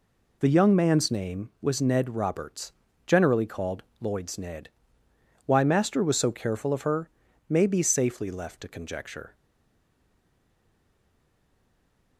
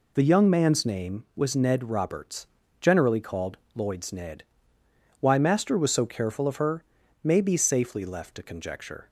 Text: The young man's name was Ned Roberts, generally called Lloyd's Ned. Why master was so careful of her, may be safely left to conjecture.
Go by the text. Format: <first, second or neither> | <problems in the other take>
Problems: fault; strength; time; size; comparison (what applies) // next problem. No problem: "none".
second | pauses between "called" and "Lloyd's"; slight; at 3.8 s; 0.18 s long; slight in the second // stays silent after the last word; strong; from 9.3 s on; 2.8 s long